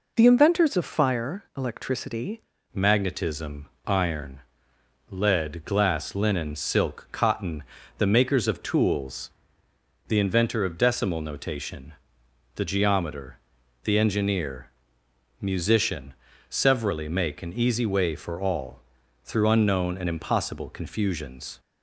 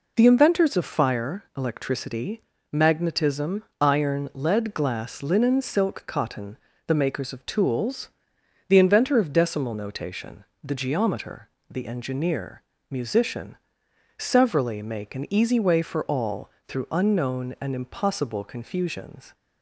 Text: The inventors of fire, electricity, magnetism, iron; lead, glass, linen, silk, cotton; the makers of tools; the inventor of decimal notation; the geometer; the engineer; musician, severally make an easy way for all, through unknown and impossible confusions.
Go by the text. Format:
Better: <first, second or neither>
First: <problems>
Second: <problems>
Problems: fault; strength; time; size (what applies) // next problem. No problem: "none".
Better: second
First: changes voice at "magnetism"; from 2.7 s on; 18.8 s long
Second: none